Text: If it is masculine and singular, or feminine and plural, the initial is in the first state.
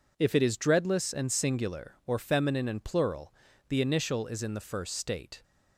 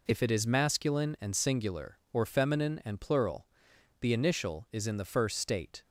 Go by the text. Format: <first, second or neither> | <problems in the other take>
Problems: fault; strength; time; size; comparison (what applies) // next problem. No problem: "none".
second | says "dreadless" for "masculine"; at 0.5 s